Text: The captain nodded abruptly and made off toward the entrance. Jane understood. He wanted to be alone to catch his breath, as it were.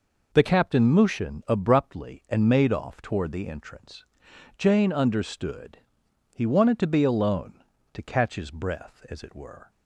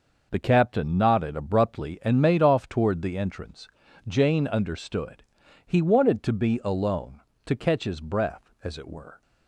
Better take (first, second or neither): second